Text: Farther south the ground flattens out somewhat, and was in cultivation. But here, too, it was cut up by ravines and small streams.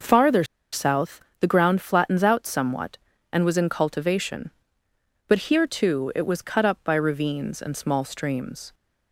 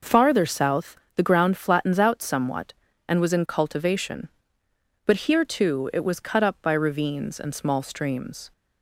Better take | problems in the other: second | pauses between "Farther" and "south"; slight; at 0.4 s; 0.29 s long // pauses between "south" and "the"; slight; at 1.2 s; 0.18 s long; slight in the second

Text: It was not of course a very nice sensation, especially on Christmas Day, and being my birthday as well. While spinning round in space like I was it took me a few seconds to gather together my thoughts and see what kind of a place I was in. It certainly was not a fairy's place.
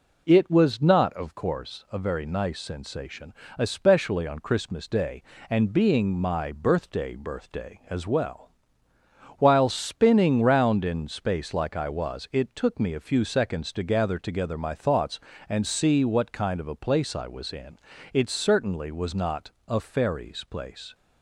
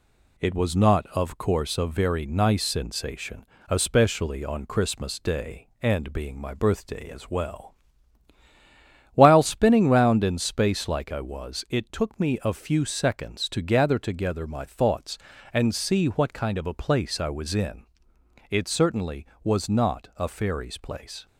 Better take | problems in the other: second | says "birthday" twice; at 7.1 s // pauses between "not" and "a"; slight; at 19.5 s; 0.16 s long

